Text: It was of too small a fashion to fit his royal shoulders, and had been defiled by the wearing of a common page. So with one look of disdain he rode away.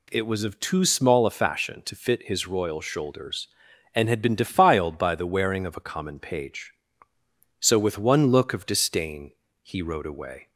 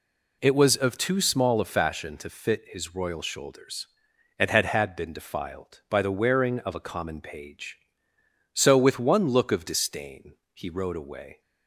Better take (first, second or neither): first